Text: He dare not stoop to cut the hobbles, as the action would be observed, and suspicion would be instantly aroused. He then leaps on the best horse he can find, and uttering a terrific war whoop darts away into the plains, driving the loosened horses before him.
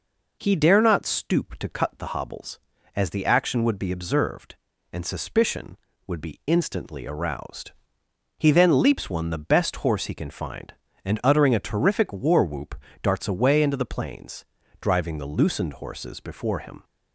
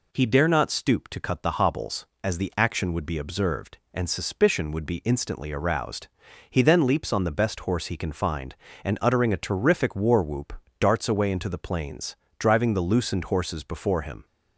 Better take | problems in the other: second | says "one" for "on"; at 9.0 s // pauses between "whoop" and "darts"; slight; at 12.7 s; 0.26 s long; slight in the second

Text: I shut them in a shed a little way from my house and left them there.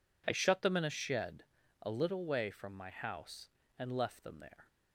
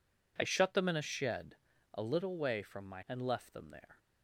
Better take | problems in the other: first | pauses between "shed" and "a"; at 1.5 s; 0.38 s long; also in the first // skips "house"; at 3.0 s

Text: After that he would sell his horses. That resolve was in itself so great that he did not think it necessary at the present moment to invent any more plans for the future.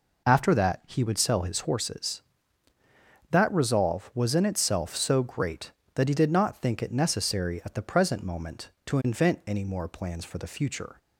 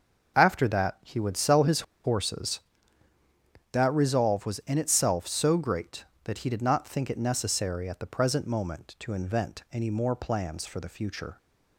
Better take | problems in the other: first | starts louder than the rest; noticeable; until 1.4 s; 6 dB // pauses between "his" and "horses"; slight; at 1.8 s; 0.21 s long

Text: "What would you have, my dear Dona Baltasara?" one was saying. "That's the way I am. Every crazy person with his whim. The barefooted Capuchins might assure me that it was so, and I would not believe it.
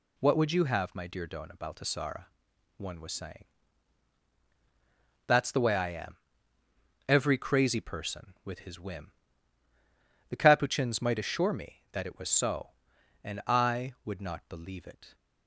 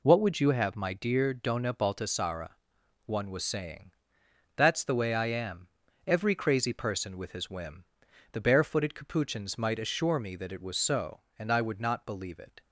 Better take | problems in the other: second | skips "barefooted"; at 10.3 s

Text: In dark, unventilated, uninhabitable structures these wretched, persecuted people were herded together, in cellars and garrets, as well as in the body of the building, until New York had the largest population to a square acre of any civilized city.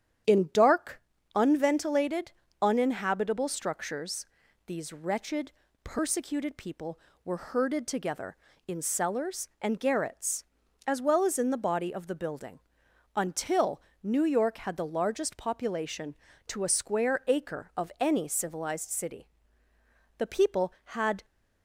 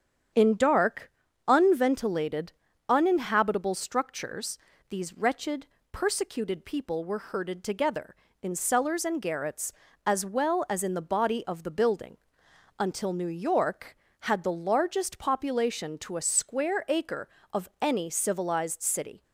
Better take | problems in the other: second | starts louder than the rest; strong; until 1.6 s; 9.5 dB; strong in the second // pauses between "structures" and "these"; at 4.2 s; 0.42 s long; slight in the second // pauses between "until" and "New"; slight; at 13.8 s; 0.20 s long // goes on to say "The people had"; noticeable; from 20.1 s on; 1.0 s long

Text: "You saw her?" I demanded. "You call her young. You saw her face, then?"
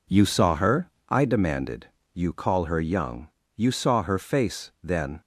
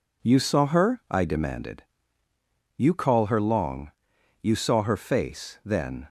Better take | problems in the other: first | says "long" for "young"; at 3.3 s

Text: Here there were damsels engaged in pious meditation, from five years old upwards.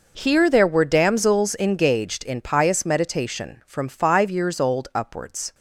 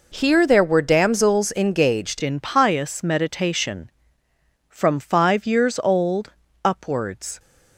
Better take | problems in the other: first | changes voice at "in"; from 2.2 s on; 5.1 s long // pauses between "old" and "upwards"; slight; at 6.3 s; 0.32 s long

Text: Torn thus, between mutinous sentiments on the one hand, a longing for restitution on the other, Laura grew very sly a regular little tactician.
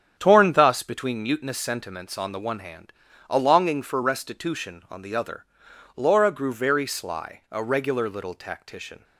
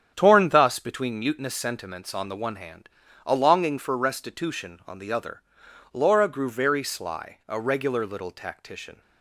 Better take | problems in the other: neither | starts louder than the rest; strong; the same in both

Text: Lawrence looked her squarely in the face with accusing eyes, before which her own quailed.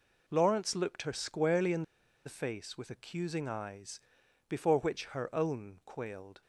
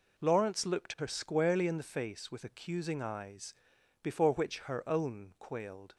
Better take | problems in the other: second | pauses between "in" and "the"; at 1.8 s; 0.43 s long

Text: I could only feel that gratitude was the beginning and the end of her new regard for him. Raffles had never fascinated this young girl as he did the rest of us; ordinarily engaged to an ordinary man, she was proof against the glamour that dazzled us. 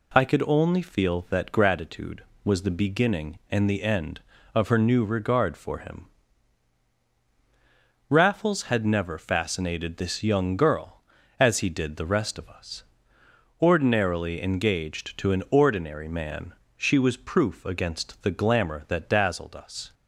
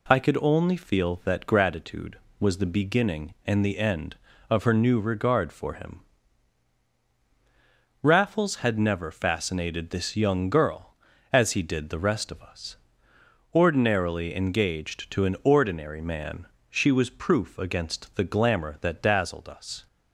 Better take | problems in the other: neither | none

